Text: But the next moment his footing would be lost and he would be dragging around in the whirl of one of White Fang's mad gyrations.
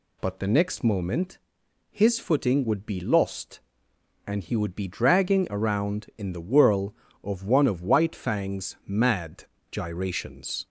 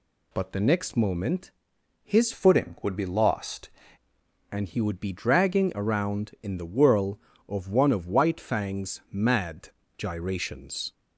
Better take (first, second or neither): first